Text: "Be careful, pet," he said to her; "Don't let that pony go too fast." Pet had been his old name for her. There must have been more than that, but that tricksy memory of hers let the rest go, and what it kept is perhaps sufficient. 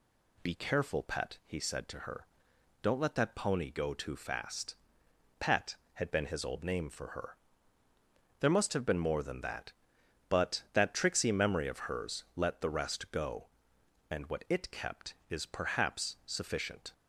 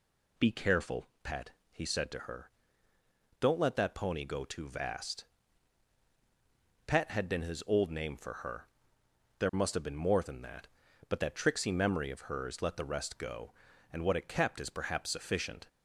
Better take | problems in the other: first | says "vast" for "fast"; at 4.6 s

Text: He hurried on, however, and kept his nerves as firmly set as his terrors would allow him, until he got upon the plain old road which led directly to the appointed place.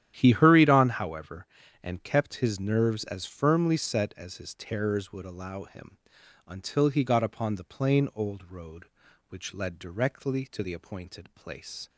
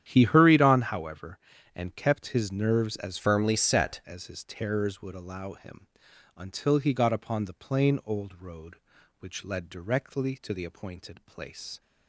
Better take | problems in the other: first | starts louder than the rest; strong; until 1.0 s; 10 dB; strong in the first // changes voice from "firmly" to "set"; from 3.1 to 3.9 s; 0.8 s long

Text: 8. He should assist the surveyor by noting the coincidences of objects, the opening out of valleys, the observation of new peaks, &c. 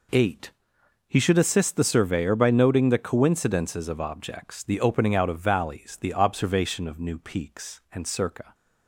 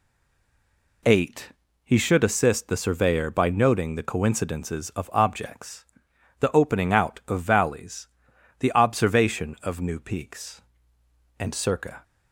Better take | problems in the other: first | stays silent before the first word; until 1.0 s; 1.0 s long

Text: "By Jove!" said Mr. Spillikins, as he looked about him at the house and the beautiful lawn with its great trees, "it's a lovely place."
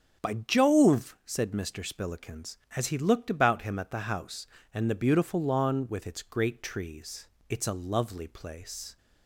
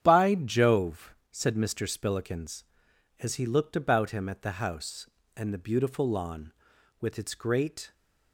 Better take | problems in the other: first | starts louder than the rest; strong; until 1.0 s; 9 dB; strong in the first // stops before "trees it's a lovely place"; at 7.9 s

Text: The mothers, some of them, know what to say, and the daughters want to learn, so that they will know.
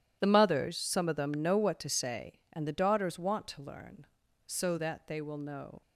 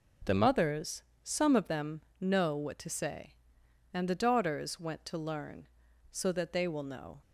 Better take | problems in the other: first | says "went" for "want"; at 4.7 s

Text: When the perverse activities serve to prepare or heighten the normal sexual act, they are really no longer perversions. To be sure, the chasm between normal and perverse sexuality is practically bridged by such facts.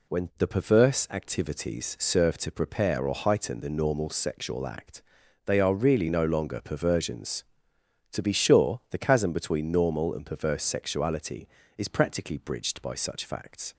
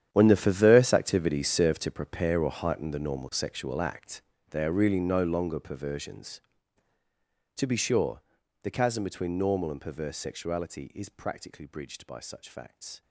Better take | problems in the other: first | gets quieter; strong; throughout; 16.5 dB

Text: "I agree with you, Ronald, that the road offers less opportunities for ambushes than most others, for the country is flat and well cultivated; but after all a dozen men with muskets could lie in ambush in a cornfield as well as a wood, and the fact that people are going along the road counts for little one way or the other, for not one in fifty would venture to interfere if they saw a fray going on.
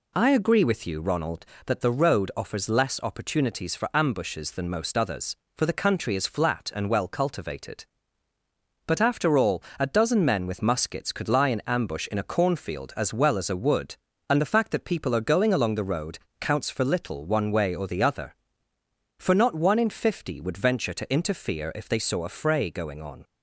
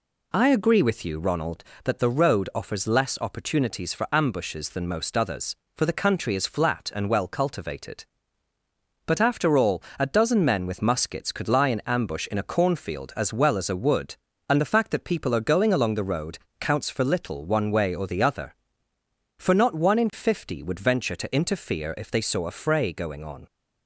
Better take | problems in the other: neither | pauses between "all" and "a"; slight; the same in both // pauses between "road" and "counts"; slight; the same in both

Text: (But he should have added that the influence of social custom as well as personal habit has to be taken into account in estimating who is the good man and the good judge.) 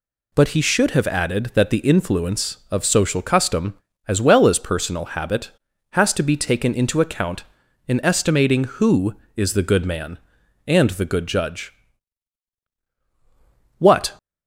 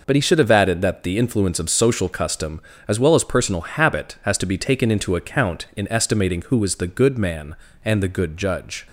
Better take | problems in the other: second | goes on to say "What"; slight; from 13.7 s on; 0.34 s long

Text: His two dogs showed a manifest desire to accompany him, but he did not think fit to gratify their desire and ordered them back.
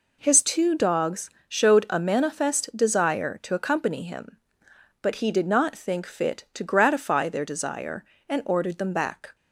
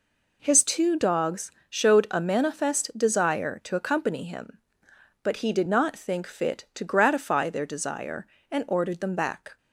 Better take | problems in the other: neither | pauses between "dogs" and "showed"; slight; the same in both

